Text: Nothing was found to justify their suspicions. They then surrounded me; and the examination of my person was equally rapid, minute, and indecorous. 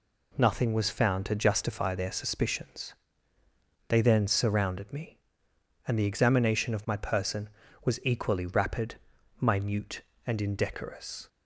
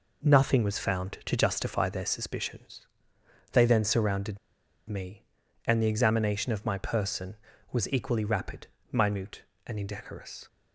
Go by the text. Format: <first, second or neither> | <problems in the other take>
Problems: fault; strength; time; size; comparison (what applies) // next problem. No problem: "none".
first | pauses between "surrounded" and "me"; noticeable; at 4.3 s; 0.49 s long